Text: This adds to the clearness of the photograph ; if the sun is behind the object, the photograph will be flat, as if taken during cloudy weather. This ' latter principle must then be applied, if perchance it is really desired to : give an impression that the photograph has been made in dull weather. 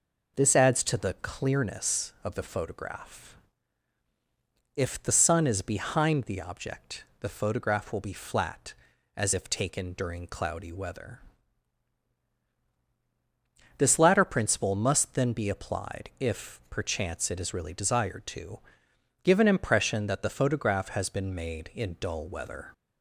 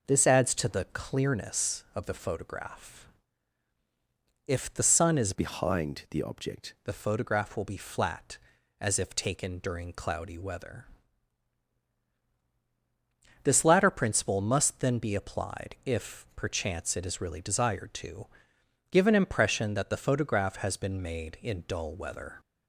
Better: first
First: none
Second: changes voice from "behind" to "object"; from 5.3 to 6.7 s; 1.4 s long

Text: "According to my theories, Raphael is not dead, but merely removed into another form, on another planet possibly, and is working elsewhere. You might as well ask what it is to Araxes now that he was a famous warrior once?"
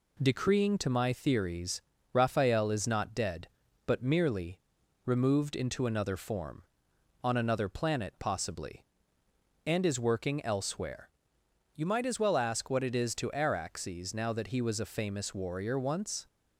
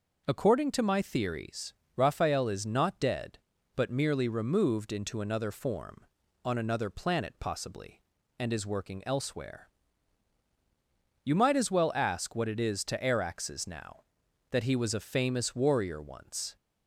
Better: second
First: says "Decreeing" for "According"; at 0.1 s // pauses between "merely" and "removed"; noticeable; at 4.5 s; 0.48 s long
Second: none

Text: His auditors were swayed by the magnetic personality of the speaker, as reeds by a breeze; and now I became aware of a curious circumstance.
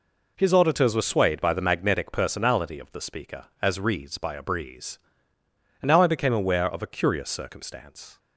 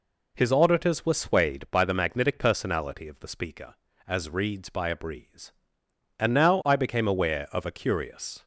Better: first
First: none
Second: stops before "circumstance"; at 8.4 s

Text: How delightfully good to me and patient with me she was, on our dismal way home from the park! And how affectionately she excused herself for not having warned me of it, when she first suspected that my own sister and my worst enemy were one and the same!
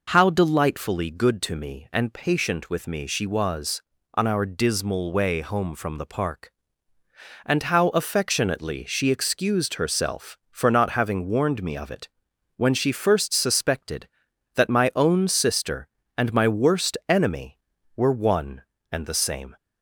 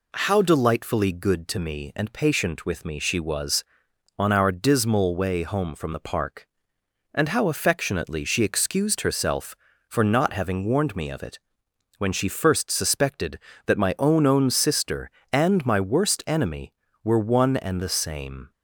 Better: first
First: none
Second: says "own" twice; at 14.2 s

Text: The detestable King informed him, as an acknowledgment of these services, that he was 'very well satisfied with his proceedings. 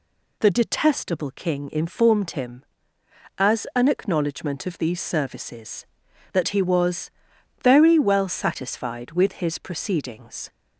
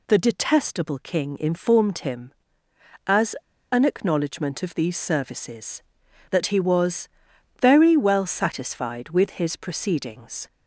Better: first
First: pauses between "was" and "very"; noticeable; at 7.1 s; 0.52 s long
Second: pauses between "as" and "an"; at 3.3 s; 0.37 s long // pauses between "was" and "very"; noticeable; at 7.0 s; 0.52 s long

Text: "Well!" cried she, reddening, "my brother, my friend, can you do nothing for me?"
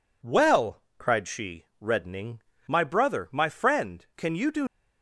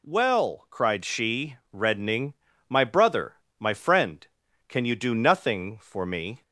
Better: second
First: stops before "nothing for me"; at 4.6 s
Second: none

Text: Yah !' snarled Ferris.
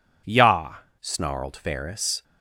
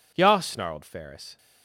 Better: second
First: changes voice at "snarled"; from 1.0 s on; 1.2 s long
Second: none

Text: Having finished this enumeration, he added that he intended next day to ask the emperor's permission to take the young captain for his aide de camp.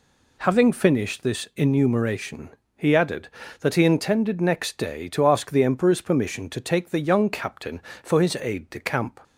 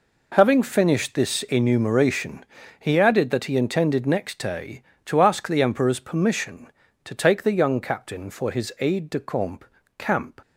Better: first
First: none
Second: says "camp" twice; at 9.9 s

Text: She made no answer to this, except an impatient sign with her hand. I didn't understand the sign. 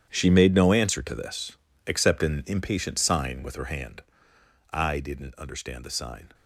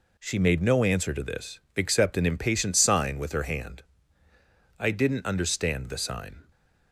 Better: second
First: gets quieter; strong; throughout; 15.5 dB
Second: none

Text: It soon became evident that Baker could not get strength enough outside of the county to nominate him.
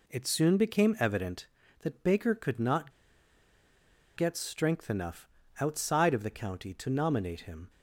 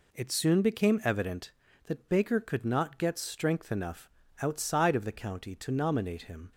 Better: second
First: pauses between "not" and "get"; at 2.9 s; 1.2 s long // pauses between "enough" and "outside"; slight; at 5.2 s; 0.32 s long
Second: pauses between "enough" and "outside"; slight; at 4.0 s; 0.32 s long

